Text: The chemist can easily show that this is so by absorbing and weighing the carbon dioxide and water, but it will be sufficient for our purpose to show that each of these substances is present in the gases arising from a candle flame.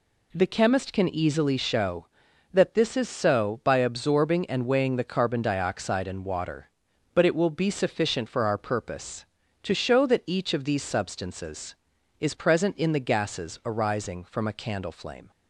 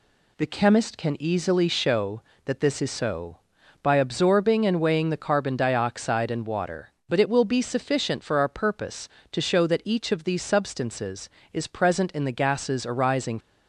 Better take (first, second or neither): first